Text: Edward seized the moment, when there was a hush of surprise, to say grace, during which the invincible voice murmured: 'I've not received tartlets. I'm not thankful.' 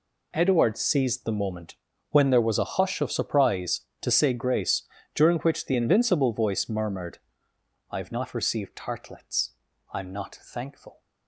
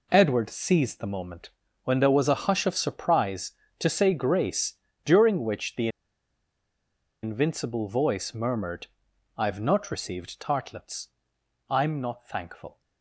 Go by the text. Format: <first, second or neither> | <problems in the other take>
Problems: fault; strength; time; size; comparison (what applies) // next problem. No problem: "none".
first | pauses between "the" and "invincible"; strong; at 5.8 s; 1.3 s long